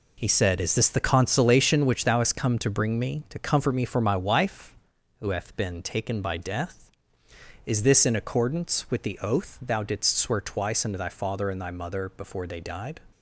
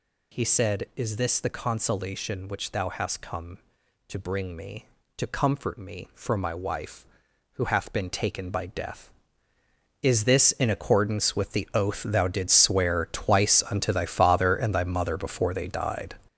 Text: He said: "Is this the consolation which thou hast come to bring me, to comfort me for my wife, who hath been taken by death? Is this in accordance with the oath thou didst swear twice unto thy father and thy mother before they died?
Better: first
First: none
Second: gets louder; strong; throughout; 7.5 dB

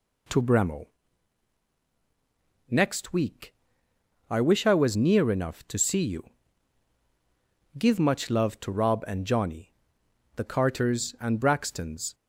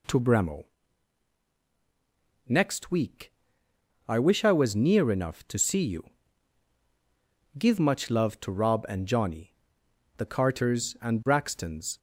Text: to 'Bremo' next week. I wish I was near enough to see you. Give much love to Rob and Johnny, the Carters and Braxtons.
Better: neither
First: pauses between "Bremo" and "next"; strong; at 0.8 s; 1.8 s long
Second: pauses between "Bremo" and "next"; strong; at 0.6 s; 1.8 s long

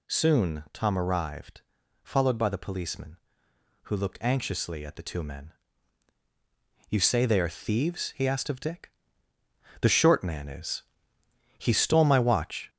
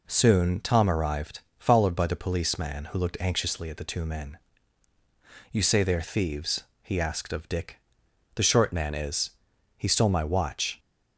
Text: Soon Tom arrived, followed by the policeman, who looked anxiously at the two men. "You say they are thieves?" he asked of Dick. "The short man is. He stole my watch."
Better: second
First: gets louder; noticeable; throughout; 4.5 dB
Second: none

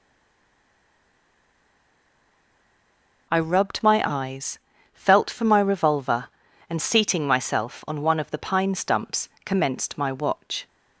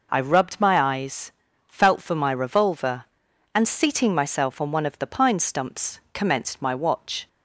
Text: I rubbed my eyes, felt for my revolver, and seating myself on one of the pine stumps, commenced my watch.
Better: second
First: stays silent before the first word; strong; until 3.2 s; 3.2 s long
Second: none

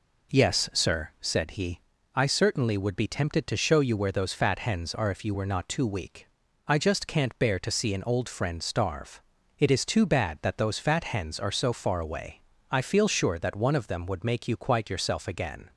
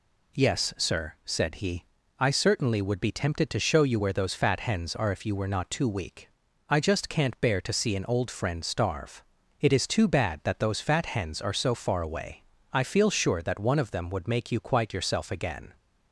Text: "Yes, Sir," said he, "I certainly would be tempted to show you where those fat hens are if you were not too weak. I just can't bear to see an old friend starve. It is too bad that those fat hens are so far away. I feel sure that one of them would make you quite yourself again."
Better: second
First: starts louder than the rest; noticeable; until 1.4 s; 4.5 dB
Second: none

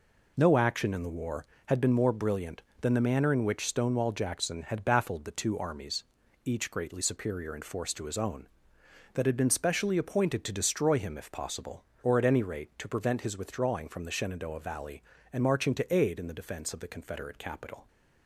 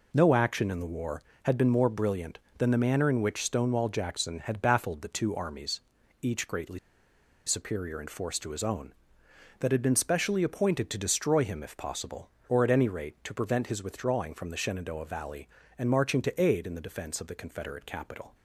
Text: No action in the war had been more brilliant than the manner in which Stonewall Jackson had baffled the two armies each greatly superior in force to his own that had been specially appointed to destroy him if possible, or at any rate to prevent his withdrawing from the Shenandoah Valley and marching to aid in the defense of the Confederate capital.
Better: first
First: pauses between "armies" and "each"; at 6.0 s; 0.40 s long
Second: pauses between "armies" and "each"; at 5.8 s; 0.40 s long // pauses between "greatly" and "superior"; noticeable; at 6.7 s; 0.67 s long

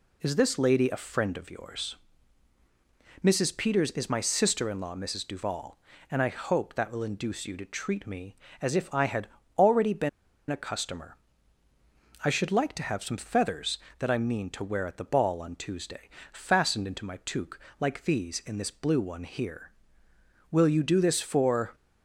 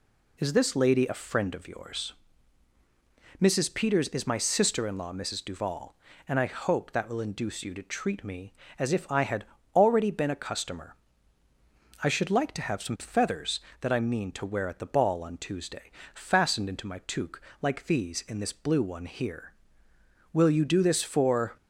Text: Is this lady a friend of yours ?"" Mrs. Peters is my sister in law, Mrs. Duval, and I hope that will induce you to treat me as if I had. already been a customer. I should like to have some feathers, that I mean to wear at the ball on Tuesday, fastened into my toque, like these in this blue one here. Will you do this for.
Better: second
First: pauses between "been" and "a"; at 10.0 s; 0.40 s long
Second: none

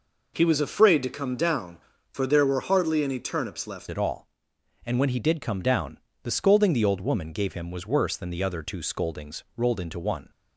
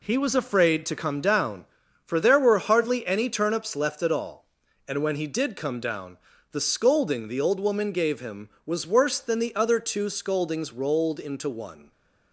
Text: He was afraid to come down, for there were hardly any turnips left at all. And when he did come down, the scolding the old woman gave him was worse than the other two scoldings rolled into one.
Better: second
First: changes voice at "at"; from 3.9 s on; 6.4 s long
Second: none

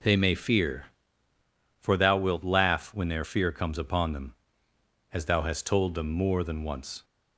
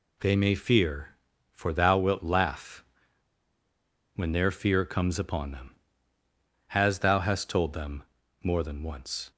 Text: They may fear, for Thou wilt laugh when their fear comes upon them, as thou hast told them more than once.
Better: first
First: none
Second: pauses between "laugh" and "when"; strong; at 2.8 s; 1.3 s long // pauses between "them" and "more"; at 8.0 s; 0.40 s long

